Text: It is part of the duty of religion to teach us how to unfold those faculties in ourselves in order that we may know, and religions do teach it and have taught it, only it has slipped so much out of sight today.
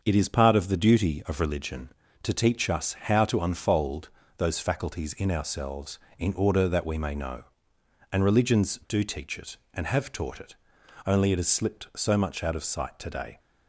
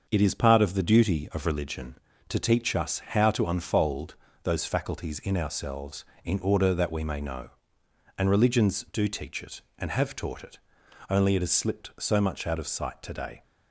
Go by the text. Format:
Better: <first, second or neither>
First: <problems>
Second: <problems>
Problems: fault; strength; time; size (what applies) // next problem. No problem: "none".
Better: neither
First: starts louder than the rest; until 1.0 s; 6.5 dB // pauses between "unfold" and "those"; slight; at 4.0 s; 0.28 s long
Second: starts louder than the rest; until 1.1 s; 6.5 dB // pauses between "unfold" and "those"; slight; at 4.1 s; 0.28 s long